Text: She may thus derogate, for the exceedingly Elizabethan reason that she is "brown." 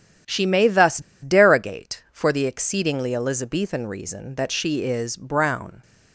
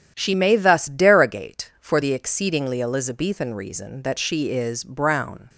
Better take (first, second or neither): second